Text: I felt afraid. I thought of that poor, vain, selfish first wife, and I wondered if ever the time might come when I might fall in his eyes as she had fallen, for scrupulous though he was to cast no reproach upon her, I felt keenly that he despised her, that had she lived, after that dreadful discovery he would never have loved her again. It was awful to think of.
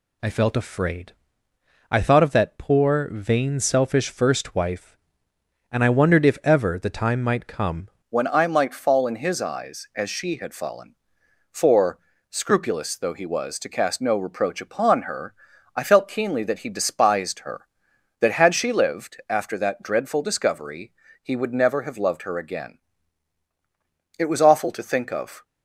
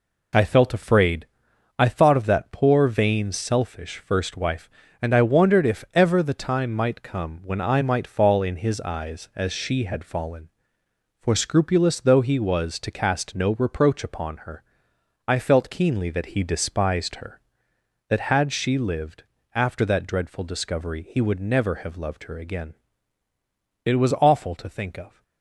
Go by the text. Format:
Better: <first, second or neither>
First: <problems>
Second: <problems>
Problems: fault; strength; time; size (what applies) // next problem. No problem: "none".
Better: second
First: changes voice at "when"; from 8.1 s on; 17.3 s long // pauses between "for" and "scrupulous"; slight; at 11.9 s; 0.32 s long // pauses between "discovery" and "he"; slight; at 20.9 s; 0.32 s long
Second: none